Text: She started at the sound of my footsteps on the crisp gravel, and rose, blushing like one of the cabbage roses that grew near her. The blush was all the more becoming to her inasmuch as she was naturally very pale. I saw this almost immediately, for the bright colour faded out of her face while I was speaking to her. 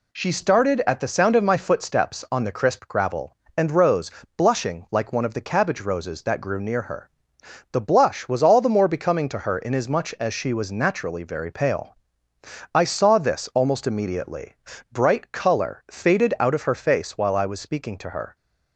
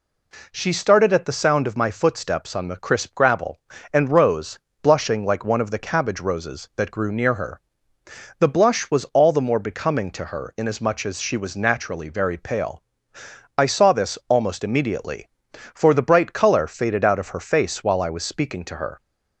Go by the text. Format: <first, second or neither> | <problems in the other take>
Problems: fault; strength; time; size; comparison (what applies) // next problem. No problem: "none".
second | skips "for the"; at 14.7 s